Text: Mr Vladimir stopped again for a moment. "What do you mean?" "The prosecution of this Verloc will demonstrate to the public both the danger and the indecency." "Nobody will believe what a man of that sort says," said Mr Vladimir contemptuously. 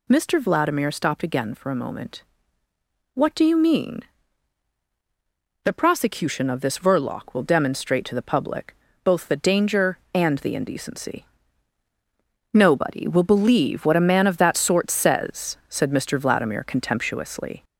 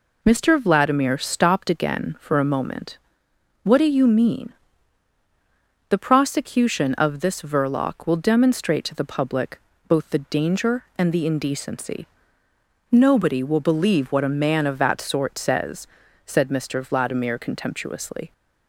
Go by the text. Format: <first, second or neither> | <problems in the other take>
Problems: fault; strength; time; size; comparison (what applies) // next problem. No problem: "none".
second | gets louder; slight; throughout; 2.5 dB // pauses between "public" and "both"; slight; at 8.7 s; 0.30 s long; slight in the second